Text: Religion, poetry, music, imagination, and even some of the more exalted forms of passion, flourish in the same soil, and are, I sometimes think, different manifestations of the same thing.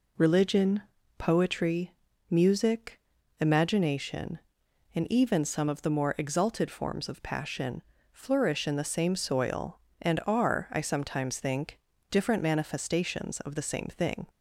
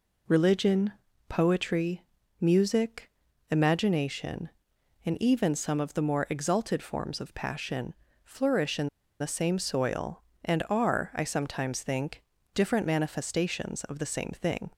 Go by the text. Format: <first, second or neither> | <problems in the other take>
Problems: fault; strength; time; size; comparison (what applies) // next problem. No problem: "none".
first | pauses between "in" and "the"; slight; at 8.8 s; 0.31 s long